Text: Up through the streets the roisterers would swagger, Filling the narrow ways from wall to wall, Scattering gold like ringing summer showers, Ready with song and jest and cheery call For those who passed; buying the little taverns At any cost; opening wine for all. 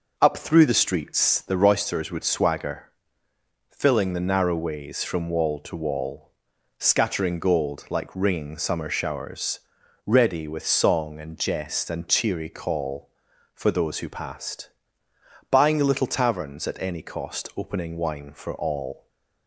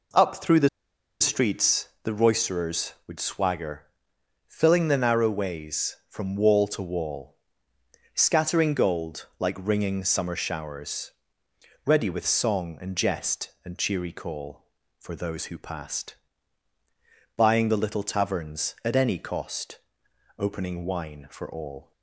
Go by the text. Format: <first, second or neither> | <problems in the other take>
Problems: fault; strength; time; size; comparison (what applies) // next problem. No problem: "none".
first | pauses between "the" and "streets"; noticeable; at 0.6 s; 0.52 s long